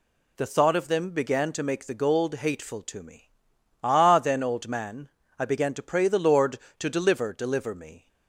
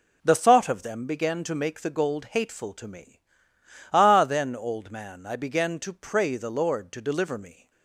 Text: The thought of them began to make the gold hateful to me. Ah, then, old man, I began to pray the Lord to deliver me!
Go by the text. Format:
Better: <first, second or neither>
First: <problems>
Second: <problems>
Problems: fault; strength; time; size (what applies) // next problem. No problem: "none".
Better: second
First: says "deliver" twice; at 7.3 s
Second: none